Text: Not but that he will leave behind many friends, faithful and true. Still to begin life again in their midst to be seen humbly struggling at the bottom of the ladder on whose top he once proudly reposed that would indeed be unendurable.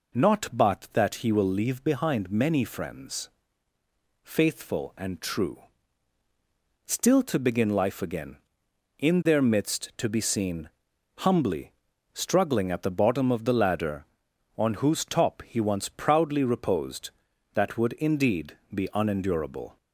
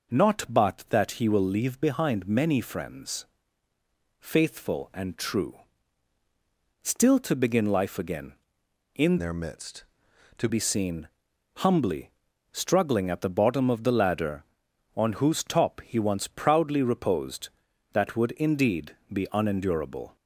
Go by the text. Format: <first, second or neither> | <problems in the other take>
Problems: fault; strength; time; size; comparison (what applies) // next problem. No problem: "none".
first | changes voice from "their" to "to"; from 9.1 to 10.4 s; 1.3 s long // pauses between "seen" and "humbly"; noticeable; at 11.0 s; 0.50 s long; noticeable in the first // pauses between "humbly" and "struggling"; at 12.0 s; 0.42 s long; also in the first // pauses between "indeed" and "be"; slight; at 18.9 s; 0.18 s long; slight in the first